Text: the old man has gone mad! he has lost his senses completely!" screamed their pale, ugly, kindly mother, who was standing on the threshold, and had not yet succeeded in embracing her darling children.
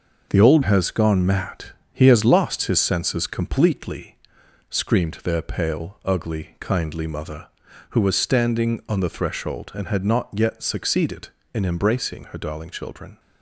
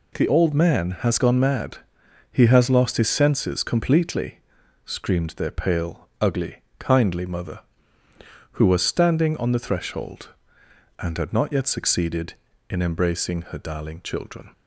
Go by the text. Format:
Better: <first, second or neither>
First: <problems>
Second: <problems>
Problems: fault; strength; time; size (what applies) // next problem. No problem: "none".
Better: second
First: skips "man"; at 0.6 s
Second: none